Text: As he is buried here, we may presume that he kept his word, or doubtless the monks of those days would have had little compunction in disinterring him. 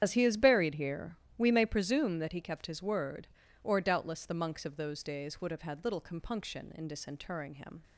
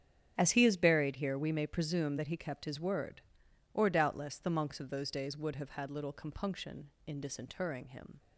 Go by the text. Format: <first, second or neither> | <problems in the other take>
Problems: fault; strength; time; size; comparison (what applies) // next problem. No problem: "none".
second | loses the start of "As"; at 0.0 s; 40 ms // starts louder than the rest; strong; until 1.0 s; 9 dB; strong in the second